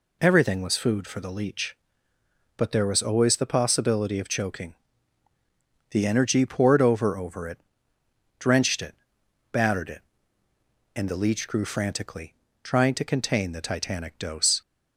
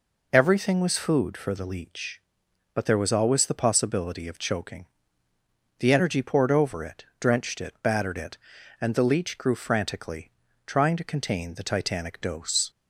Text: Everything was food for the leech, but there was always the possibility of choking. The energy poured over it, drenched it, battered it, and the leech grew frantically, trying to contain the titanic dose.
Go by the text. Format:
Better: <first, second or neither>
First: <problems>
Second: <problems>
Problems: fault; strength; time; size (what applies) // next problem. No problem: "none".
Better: second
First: says "over" twice; at 7.1 s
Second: none